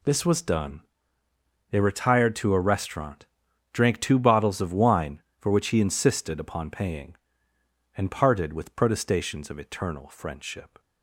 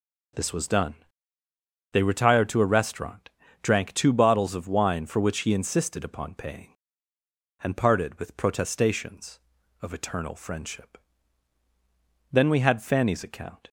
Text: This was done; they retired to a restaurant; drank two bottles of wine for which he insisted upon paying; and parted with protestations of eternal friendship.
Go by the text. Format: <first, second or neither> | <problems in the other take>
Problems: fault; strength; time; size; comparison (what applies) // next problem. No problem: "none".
first | goes on to say "Then we had Fanny's account"; from 12.3 s on; 1.3 s long